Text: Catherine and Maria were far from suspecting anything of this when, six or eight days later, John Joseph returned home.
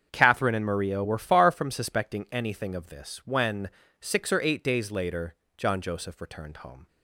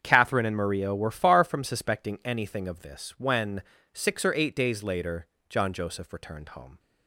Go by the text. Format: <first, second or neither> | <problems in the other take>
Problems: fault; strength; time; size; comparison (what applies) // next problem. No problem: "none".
neither | starts louder than the rest; strong; the same in both